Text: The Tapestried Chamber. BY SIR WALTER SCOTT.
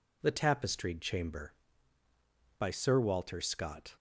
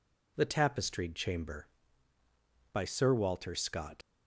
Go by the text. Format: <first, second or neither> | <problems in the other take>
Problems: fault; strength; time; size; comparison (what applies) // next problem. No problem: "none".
first | leaves "SCOTT" unfinished; at 4.0 s; 90 ms